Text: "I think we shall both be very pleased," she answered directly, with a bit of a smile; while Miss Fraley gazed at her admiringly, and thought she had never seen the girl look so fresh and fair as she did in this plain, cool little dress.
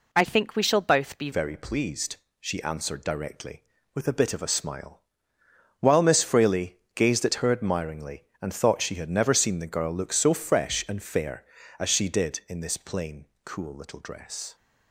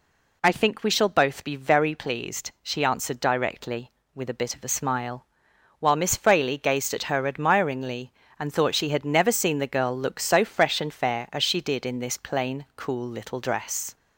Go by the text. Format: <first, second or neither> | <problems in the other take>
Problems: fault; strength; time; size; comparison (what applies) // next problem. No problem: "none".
second | changes voice at "very"; from 1.3 s on; 13.2 s long // pauses between "Fraley" and "gazed"; slight; at 6.7 s; 0.16 s long